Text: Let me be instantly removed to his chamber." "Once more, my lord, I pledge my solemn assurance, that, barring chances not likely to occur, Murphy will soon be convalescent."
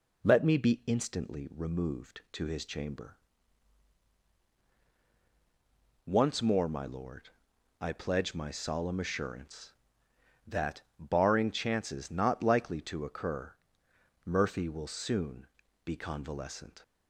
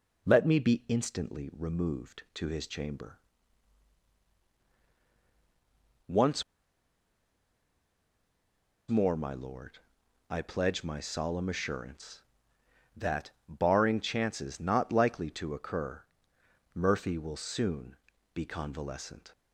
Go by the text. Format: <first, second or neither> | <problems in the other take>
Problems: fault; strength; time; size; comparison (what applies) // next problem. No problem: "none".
first | pauses between "Once" and "more"; strong; at 6.4 s; 2.4 s long // pauses between "soon" and "be"; at 17.9 s; 0.38 s long; also in the first